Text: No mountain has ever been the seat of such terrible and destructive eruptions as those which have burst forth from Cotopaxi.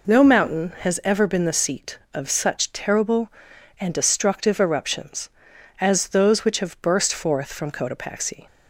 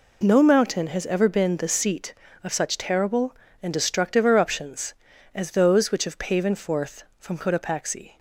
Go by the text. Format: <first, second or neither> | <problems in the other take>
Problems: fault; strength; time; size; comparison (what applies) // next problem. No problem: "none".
first | says "paven" for "burst"; at 6.1 s